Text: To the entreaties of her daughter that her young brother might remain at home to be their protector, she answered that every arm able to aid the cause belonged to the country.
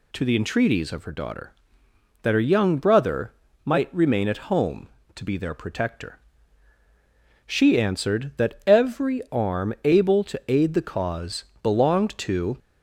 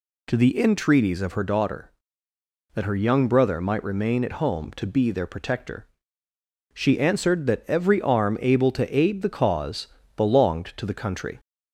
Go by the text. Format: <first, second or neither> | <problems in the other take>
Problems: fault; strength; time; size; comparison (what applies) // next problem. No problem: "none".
second | pauses between "brother" and "might"; slight; at 3.3 s; 0.32 s long // pauses between "cause" and "belonged"; slight; at 11.4 s; 0.18 s long; slight in the second // stops before "the country"; at 12.5 s